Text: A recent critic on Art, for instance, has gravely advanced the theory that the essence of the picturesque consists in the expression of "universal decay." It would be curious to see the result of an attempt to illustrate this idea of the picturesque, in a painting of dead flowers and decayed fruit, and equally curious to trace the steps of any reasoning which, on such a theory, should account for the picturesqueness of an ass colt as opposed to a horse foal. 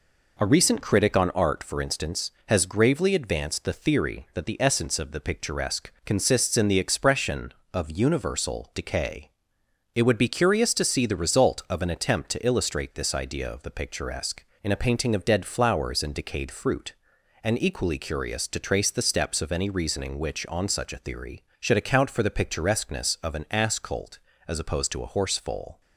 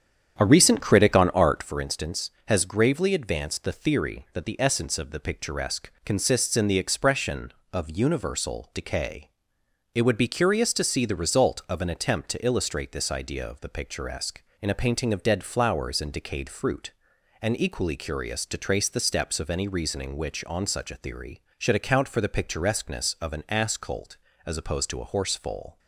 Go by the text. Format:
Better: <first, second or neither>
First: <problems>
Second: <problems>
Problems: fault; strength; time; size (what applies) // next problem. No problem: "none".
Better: first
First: pauses between "picturesque" and "consists"; slight; at 5.8 s; 0.16 s long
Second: starts louder than the rest; strong; until 1.7 s; 8.5 dB // pauses between "picturesque" and "consists"; slight; at 5.8 s; 0.16 s long